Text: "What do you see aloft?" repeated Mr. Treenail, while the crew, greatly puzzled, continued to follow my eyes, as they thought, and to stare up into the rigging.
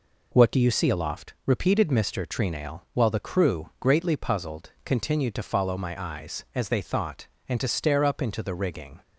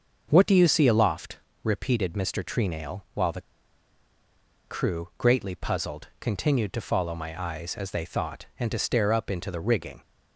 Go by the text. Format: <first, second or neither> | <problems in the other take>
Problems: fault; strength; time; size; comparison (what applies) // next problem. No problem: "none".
first | starts louder than the rest; until 1.3 s; 6.5 dB // pauses between "the" and "crew"; strong; at 3.4 s; 1.2 s long